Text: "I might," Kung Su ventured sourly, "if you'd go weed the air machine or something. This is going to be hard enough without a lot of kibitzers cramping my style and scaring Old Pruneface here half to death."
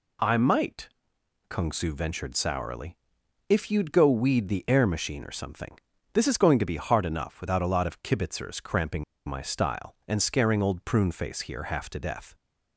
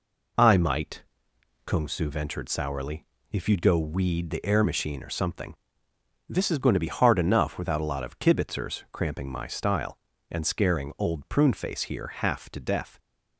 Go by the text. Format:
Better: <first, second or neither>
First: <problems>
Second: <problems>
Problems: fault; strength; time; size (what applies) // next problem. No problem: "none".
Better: second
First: pauses between "cramping" and "my"; slight; at 9.0 s; 0.24 s long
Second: none